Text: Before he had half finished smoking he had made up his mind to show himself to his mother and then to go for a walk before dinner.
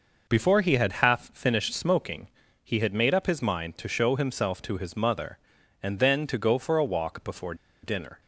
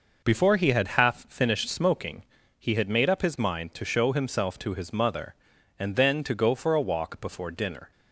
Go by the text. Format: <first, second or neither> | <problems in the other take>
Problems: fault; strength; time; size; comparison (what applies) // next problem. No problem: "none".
second | pauses between "smoking" and "he"; slight; at 2.2 s; 0.34 s long; slight in the second // pauses between "before" and "dinner"; slight; at 7.5 s; 0.28 s long